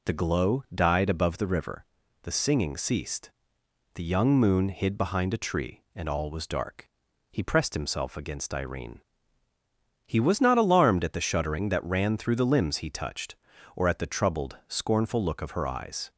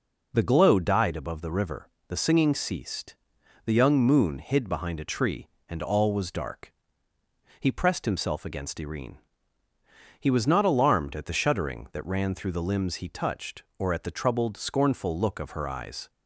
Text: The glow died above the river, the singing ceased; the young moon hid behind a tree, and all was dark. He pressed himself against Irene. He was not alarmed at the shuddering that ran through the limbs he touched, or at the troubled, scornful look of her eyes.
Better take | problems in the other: neither | none

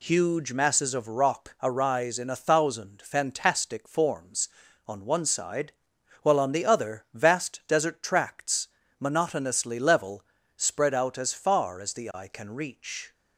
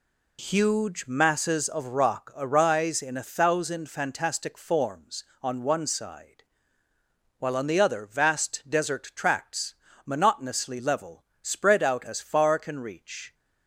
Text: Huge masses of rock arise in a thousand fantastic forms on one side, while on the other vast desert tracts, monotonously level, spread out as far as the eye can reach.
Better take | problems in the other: first | skips "as the eye"; at 12.5 s

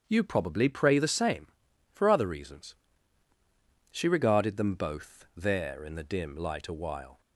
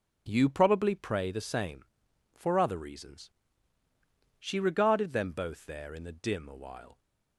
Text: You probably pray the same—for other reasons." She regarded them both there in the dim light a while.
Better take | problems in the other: first | starts louder than the rest; until 1.2 s; 7 dB; strong in the first // skips "light"; at 6.4 s

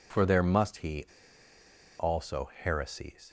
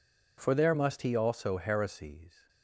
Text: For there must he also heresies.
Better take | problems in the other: second | pauses between "he" and "also"; noticeable; at 1.0 s; 0.94 s long

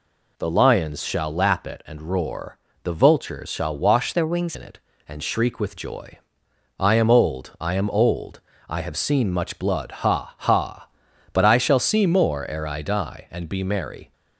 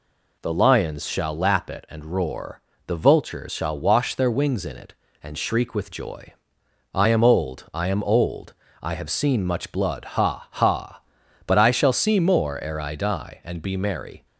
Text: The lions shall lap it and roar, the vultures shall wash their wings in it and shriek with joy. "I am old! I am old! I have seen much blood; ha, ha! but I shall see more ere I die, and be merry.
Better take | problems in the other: second | changes voice from "their" to "wings"; from 4.1 to 4.5 s; 0.4 s long

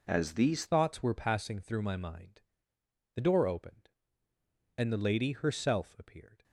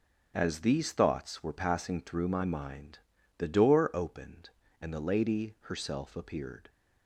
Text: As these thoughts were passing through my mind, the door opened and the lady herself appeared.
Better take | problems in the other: second | changes voice at "thoughts"; from 0.6 s on; 5.8 s long

